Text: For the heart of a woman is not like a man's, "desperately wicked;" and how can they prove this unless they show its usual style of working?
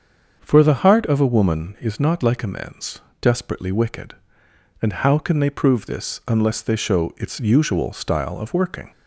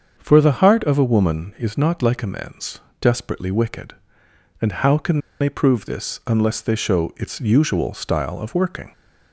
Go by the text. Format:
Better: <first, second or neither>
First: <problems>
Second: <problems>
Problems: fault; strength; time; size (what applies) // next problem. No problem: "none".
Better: first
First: starts louder than the rest; until 1.4 s; 7 dB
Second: starts louder than the rest; until 1.1 s; 7 dB // pauses between "can" and "they"; slight; at 5.1 s; 0.20 s long